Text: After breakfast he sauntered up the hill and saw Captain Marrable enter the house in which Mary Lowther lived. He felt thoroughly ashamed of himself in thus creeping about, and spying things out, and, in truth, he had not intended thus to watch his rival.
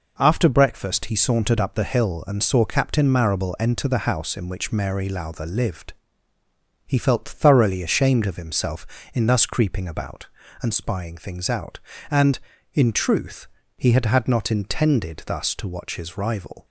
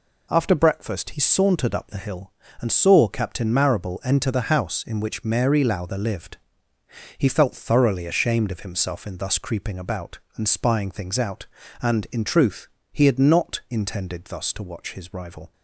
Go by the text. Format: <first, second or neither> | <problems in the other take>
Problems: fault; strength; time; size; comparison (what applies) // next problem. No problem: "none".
second | says "had" twice; at 14.0 s